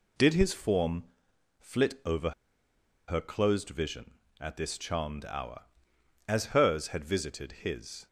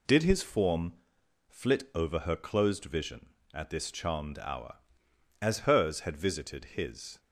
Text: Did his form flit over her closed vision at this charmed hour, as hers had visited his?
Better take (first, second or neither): second